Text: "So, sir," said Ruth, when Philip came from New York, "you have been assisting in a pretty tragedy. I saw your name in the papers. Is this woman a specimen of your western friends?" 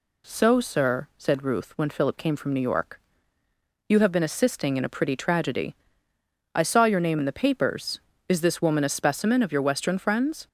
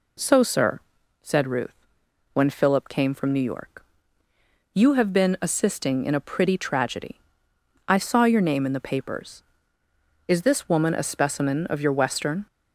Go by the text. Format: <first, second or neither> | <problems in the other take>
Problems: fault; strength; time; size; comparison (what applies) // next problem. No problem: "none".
first | stops before "friends"; at 12.4 s